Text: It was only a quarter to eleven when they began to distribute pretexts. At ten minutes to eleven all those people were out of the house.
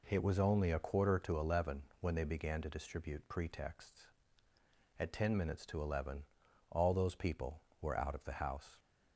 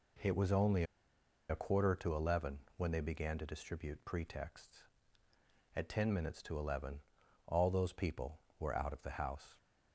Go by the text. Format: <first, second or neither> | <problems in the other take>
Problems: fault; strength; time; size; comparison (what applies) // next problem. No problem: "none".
first | pauses between "only" and "a"; noticeable; at 0.8 s; 0.66 s long // pauses between "eleven" and "when"; slight; at 2.6 s; 0.16 s long; slight in the first // pauses between "eleven" and "all"; noticeable; at 7.0 s; 0.46 s long; noticeable in the first